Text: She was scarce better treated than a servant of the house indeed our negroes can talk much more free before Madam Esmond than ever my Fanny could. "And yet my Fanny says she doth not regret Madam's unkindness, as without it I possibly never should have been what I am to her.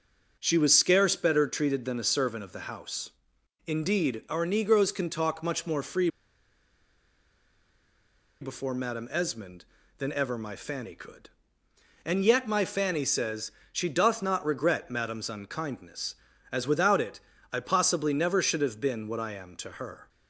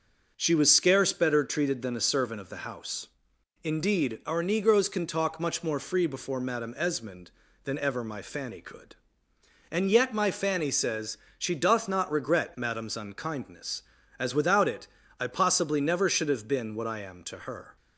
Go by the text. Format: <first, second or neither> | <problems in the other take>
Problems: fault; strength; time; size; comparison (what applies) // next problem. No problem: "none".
second | pauses between "house" and "indeed"; noticeable; at 3.0 s; 0.56 s long; noticeable in the second // pauses between "free" and "before"; strong; at 6.0 s; 2.3 s long // pauses between "says" and "she"; slight; at 13.5 s; 0.22 s long; slight in the second // pauses between "it" and "I"; slight; at 17.1 s; 0.34 s long; slight in the second